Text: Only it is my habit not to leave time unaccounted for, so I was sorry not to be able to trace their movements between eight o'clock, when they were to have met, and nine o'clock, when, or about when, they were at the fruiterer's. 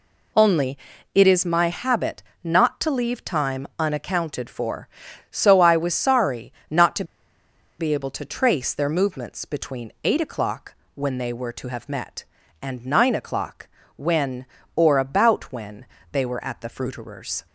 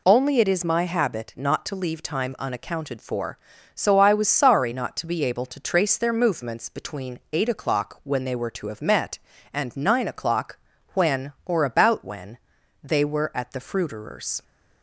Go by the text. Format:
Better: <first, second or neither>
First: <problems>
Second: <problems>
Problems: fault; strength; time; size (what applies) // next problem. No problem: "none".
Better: second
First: pauses between "Only" and "it"; slight; at 0.7 s; 0.36 s long // pauses between "habit" and "not"; slight; at 2.2 s; 0.20 s long // pauses between "sorry" and "not"; slight; at 6.5 s; 0.18 s long // pauses between "to" and "be"; noticeable; at 7.0 s; 0.75 s long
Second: none